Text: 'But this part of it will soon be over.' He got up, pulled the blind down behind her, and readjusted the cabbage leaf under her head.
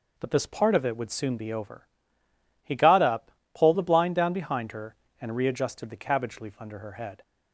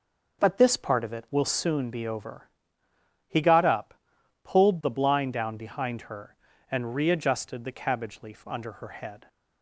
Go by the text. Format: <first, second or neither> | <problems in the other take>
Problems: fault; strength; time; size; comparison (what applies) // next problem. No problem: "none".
second | says "would" for "will"; at 0.9 s